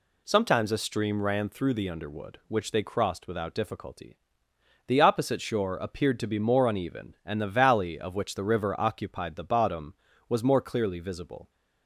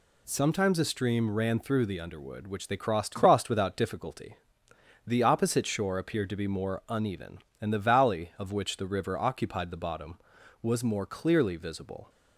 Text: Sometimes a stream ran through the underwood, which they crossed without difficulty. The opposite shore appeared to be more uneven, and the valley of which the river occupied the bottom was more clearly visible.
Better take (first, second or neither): first